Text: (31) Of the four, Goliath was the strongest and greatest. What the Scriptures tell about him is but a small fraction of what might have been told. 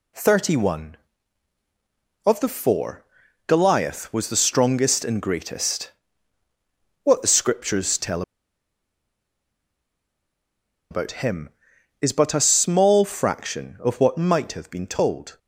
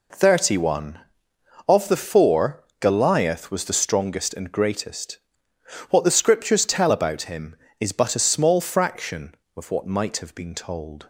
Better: second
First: pauses between "tell" and "about"; strong; at 8.2 s; 2.6 s long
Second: none

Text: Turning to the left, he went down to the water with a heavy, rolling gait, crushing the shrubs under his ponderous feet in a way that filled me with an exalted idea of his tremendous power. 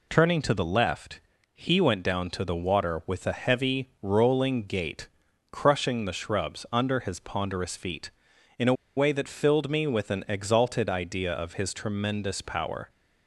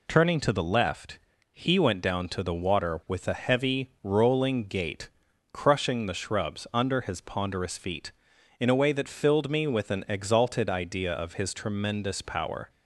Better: second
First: pauses between "a" and "way"; slight; at 8.7 s; 0.22 s long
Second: none

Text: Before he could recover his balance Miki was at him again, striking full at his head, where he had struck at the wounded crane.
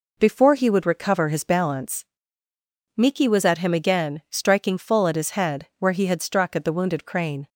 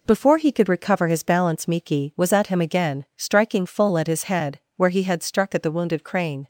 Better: second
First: says "would" for "could"; at 0.6 s // pauses between "balance" and "Miki"; noticeable; at 2.0 s; 0.92 s long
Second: none

